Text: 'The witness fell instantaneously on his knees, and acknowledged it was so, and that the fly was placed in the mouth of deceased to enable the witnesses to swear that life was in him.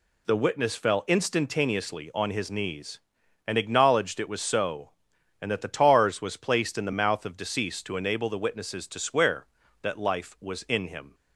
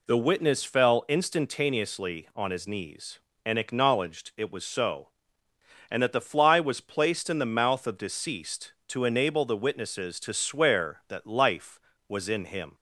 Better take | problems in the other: second | says "tars" for "fly"; at 5.6 s

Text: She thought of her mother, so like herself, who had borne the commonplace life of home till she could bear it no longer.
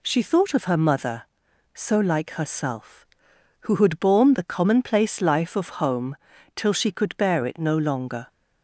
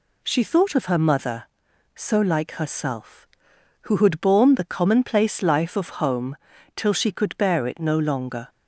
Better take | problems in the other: neither | pauses between "home" and "till"; the same in both

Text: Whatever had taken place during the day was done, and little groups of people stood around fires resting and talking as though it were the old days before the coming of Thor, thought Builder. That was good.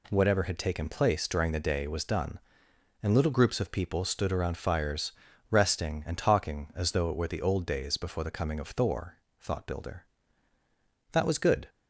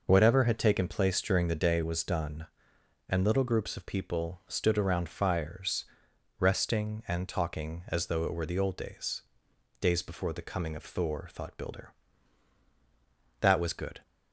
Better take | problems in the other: first | pauses between "fires" and "resting"; noticeable; at 5.8 s; 0.54 s long; also in the first // says "days" twice; at 9.7 s

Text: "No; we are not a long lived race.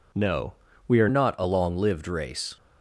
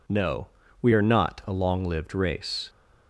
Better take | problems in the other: second | changes voice at "not"; from 1.0 s on; 1.5 s long

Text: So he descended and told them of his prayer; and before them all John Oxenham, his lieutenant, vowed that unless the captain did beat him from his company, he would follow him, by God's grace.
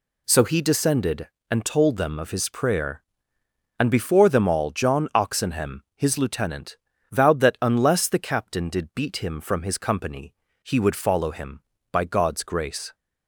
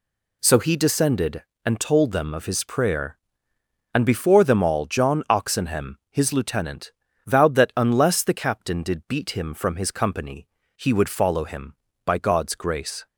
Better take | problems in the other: neither | none

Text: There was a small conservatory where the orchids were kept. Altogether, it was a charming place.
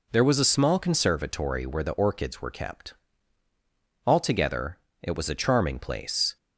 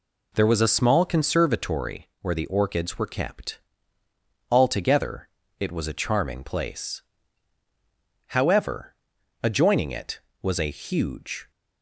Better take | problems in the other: first | pauses between "conservatory" and "where"; slight; at 2.0 s; 0.16 s long // goes on to say "However adjoining it was a huge"; strong; from 8.2 s on; 3.2 s long

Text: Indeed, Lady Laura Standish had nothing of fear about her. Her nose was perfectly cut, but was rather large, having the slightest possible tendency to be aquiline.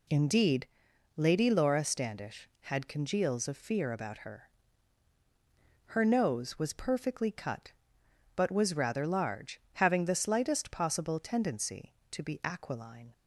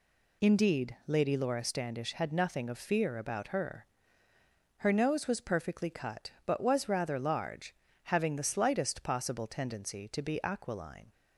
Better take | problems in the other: second | says "congeals" for "nothing"; at 2.8 s

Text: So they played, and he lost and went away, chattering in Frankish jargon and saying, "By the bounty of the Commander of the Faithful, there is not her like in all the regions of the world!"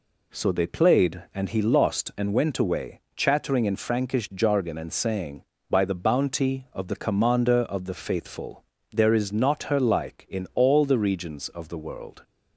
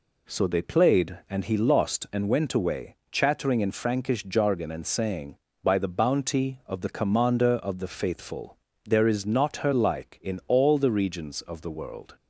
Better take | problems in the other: neither | none

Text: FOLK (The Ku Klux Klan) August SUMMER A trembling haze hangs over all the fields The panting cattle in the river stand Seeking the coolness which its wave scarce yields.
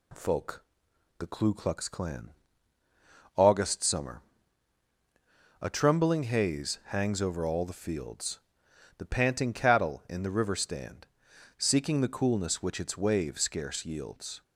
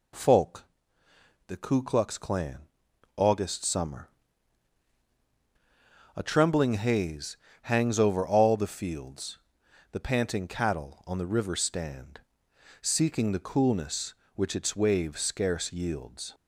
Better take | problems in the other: first | pauses between "SUMMER" and "A"; strong; at 4.0 s; 2.0 s long; strong in the first // pauses between "haze" and "hangs"; slight; at 7.3 s; 0.26 s long // pauses between "fields" and "The"; noticeable; at 9.3 s; 0.52 s long; noticeable in the first // says "on" for "in"; at 11.0 s // pauses between "stand" and "Seeking"; noticeable; at 12.2 s; 0.60 s long; noticeable in the first

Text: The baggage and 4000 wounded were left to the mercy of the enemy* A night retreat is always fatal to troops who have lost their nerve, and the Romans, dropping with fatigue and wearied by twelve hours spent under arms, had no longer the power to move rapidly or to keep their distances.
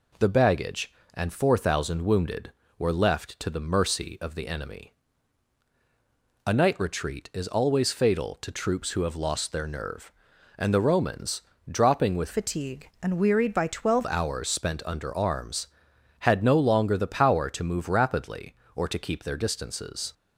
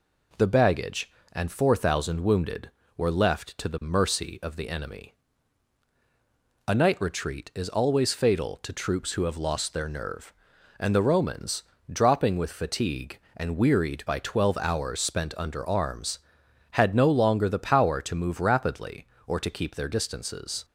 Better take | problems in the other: second | pauses between "enemy" and "A"; strong; at 4.9 s; 1.5 s long; strong in the second // changes voice from "fatigue" to "twelve"; from 12.3 to 14.0 s; 1.7 s long

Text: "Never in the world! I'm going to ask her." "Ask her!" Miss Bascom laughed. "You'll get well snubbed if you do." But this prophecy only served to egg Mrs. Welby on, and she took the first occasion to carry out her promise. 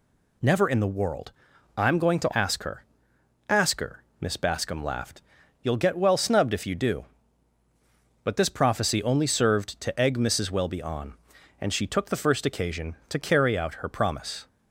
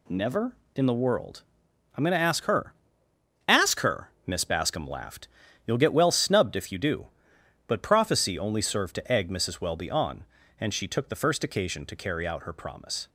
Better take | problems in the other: first | skips "this"; at 7.8 s

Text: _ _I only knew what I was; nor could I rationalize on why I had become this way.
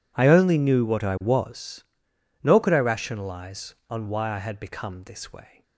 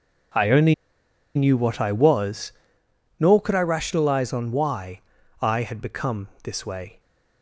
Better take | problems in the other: first | pauses between "only" and "knew"; noticeable; at 0.7 s; 0.61 s long // pauses between "why" and "I"; at 4.9 s; 0.42 s long // pauses between "become" and "this"; slight; at 6.2 s; 0.16 s long

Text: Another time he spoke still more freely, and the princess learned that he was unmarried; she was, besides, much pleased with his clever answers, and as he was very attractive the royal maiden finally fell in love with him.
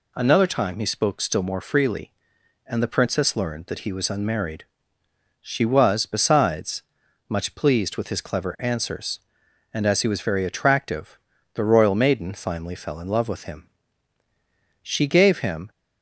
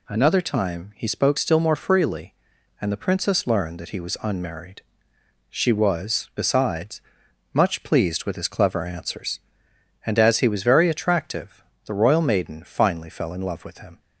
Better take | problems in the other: second | pauses between "attractive" and "the"; slight; at 11.1 s; 0.34 s long; slight in the second // goes on to say "She gave him"; noticeable; from 14.8 s on; 0.88 s long

